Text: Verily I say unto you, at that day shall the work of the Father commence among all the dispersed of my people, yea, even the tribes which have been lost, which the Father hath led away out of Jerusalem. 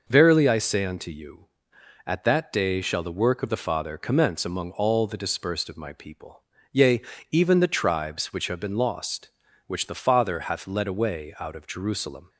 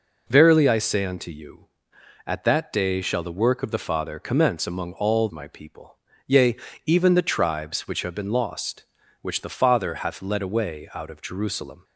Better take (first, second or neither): first